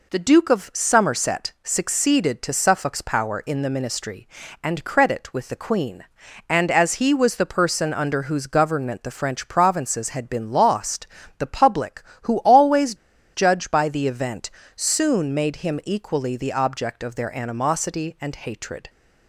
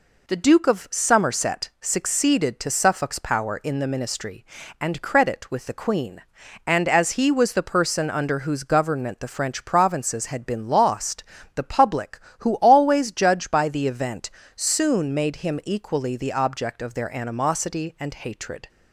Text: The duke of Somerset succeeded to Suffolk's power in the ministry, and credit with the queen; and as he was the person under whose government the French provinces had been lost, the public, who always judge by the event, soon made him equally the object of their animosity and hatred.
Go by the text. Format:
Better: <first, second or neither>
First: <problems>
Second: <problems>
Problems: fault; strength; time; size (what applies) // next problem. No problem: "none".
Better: second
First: pauses between "always" and "judge"; at 12.9 s; 0.39 s long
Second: none